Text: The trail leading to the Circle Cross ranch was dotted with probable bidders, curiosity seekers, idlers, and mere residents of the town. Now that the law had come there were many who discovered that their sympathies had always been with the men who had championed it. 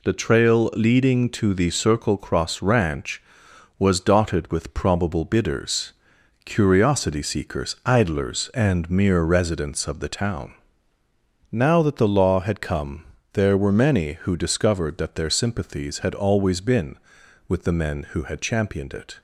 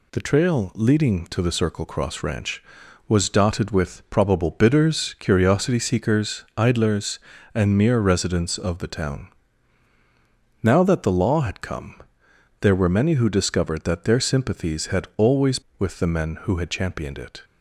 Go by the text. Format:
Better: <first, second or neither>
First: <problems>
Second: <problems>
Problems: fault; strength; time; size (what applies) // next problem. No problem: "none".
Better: first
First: pauses between "come" and "there"; slight; at 13.0 s; 0.28 s long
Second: pauses between "come" and "there"; noticeable; at 11.9 s; 0.62 s long // skips "been"; at 15.6 s